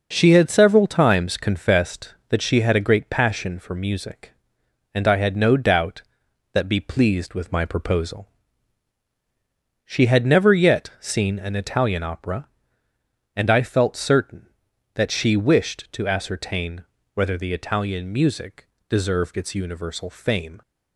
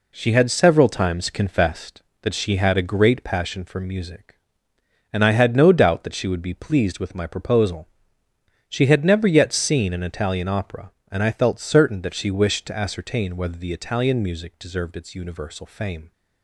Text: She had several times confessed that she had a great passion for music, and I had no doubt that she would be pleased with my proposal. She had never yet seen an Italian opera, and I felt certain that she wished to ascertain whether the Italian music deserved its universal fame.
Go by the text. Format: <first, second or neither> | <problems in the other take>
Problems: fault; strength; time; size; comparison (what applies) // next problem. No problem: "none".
second | skips "she would"; at 6.6 s // pauses between "ascertain" and "whether"; slight; at 16.8 s; 0.30 s long // pauses between "music" and "deserved"; slight; at 18.6 s; 0.22 s long